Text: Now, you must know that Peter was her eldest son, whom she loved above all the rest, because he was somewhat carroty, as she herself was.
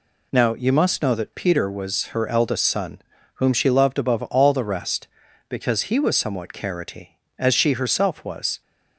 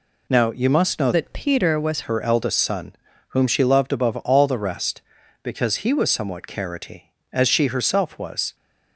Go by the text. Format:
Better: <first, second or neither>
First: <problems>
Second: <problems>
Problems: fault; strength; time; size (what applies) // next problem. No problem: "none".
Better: first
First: none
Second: changes voice from "that" to "was"; from 1.1 to 2.0 s; 0.9 s long